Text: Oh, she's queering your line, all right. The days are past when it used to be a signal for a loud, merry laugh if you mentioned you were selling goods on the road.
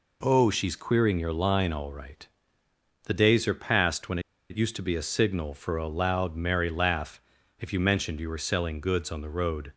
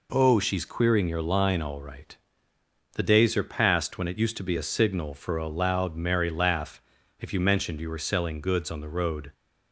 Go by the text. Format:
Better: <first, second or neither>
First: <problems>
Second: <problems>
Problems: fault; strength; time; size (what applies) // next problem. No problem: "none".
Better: second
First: pauses between "when" and "it"; slight; at 4.1 s; 0.30 s long // pauses between "laugh" and "if"; at 7.2 s; 0.38 s long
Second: pauses between "laugh" and "if"; at 6.8 s; 0.38 s long